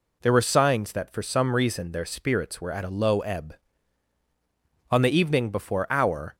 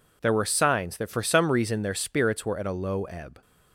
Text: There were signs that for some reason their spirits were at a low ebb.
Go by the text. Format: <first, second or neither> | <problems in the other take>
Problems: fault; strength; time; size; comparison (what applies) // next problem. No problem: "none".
second | goes on to say "On the evening before our"; from 4.9 s on; 1.4 s long